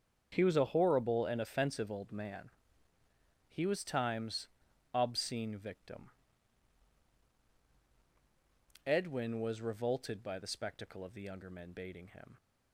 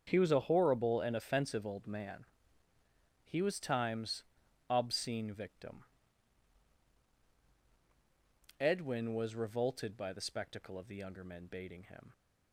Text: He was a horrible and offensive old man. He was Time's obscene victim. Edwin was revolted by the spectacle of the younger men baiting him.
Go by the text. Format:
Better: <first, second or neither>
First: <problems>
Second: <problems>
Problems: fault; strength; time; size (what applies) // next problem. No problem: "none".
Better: neither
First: starts louder than the rest; strong; until 1.3 s; 7.5 dB // pauses between "Time's" and "obscene"; noticeable; at 4.4 s; 0.48 s long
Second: starts louder than the rest; strong; until 1.0 s; 7.5 dB // pauses between "Time's" and "obscene"; noticeable; at 4.2 s; 0.48 s long